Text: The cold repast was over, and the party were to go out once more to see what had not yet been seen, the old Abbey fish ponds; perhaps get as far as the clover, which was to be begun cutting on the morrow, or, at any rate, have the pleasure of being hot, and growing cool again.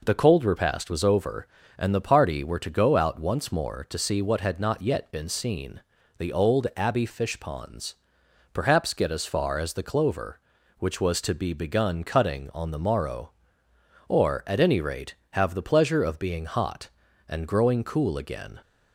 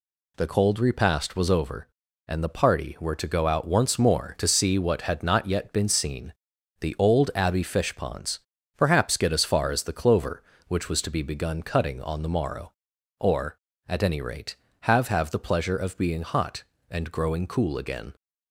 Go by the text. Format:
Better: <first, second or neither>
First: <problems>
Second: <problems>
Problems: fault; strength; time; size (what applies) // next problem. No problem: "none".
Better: first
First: none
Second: says "have" twice; at 15.0 s